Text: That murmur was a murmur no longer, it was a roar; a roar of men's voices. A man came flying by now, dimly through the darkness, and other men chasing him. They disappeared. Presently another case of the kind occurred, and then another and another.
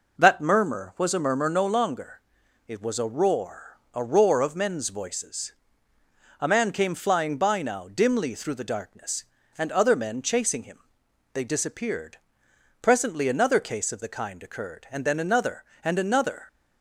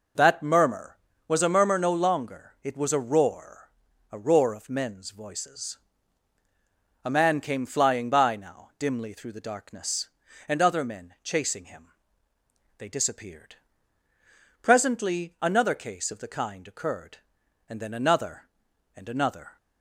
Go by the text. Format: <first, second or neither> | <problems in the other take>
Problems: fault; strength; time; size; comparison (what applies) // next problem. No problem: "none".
neither | none